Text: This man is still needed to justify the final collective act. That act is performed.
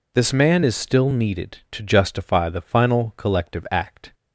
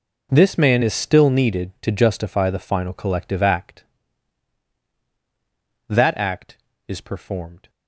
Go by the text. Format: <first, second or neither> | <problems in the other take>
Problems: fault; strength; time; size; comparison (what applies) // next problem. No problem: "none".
second | stops before "That act is performed"; at 4.1 s